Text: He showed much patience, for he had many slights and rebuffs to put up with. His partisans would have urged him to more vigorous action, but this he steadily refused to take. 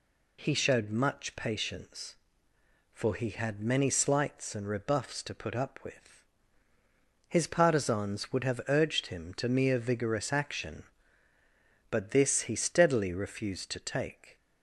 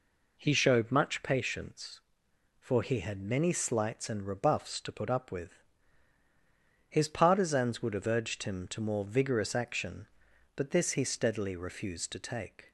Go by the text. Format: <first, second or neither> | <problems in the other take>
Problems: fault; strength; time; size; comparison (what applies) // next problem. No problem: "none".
second | says "mere" for "more"; at 9.4 s